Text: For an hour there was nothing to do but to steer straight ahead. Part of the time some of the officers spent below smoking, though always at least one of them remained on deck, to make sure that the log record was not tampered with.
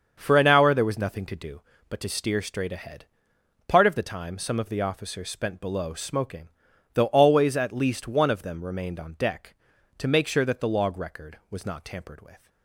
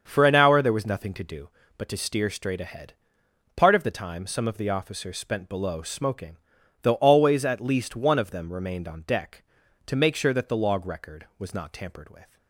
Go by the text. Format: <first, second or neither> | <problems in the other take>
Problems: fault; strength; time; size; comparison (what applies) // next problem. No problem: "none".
neither | starts louder than the rest; the same in both